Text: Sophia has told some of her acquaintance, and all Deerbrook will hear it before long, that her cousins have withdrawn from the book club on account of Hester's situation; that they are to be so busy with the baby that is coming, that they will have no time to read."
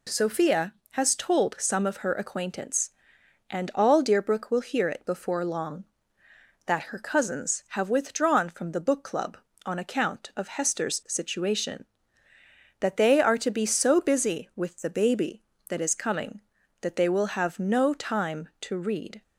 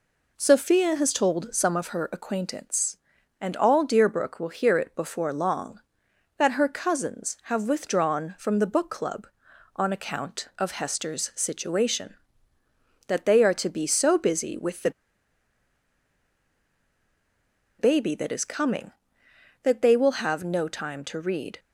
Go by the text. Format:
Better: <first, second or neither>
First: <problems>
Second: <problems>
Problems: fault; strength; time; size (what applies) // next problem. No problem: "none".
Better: first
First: none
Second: pauses between "the" and "baby"; strong; at 14.9 s; 2.8 s long